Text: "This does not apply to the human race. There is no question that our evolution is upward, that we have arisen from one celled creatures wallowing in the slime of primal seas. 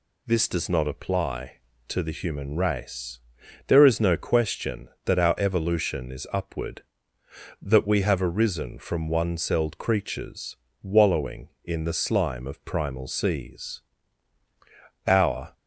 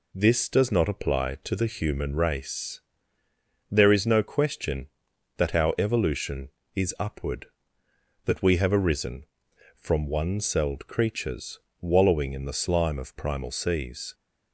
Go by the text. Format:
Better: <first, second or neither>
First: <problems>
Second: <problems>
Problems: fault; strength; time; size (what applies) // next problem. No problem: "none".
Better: second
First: pauses between "creatures" and "wallowing"; slight; at 10.5 s; 0.28 s long // goes on to say "Our"; slight; from 15.0 s on; 0.46 s long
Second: pauses between "creatures" and "wallowing"; slight; at 11.5 s; 0.22 s long